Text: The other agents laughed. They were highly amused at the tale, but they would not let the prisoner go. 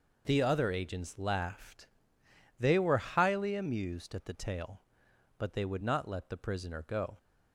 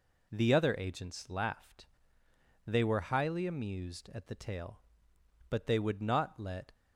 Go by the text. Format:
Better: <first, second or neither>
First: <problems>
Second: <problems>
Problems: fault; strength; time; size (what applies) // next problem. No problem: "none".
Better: first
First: none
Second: stops before "the prisoner go"; at 6.7 s